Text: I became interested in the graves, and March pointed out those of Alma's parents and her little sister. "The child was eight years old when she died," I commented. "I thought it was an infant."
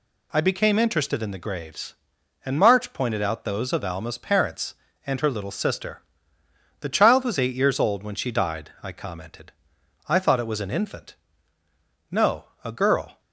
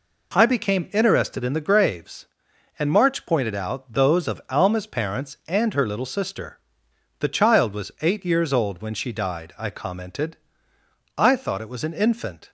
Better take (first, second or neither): second